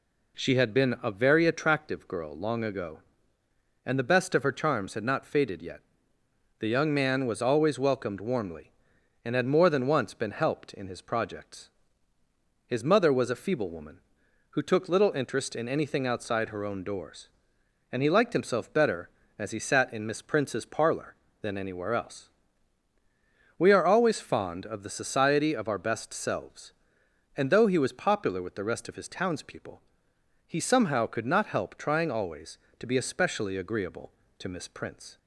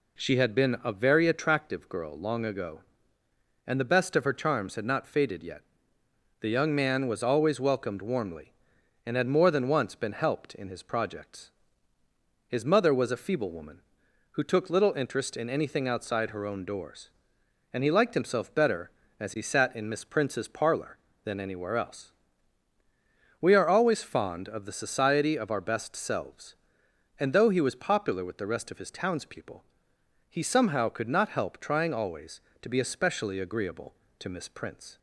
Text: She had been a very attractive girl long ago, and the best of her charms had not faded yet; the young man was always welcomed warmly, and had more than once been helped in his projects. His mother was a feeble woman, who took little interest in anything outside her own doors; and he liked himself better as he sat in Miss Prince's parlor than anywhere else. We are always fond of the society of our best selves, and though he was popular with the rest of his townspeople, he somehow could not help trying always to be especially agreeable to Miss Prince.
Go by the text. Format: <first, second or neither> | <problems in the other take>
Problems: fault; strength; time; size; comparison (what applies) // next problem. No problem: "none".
neither | none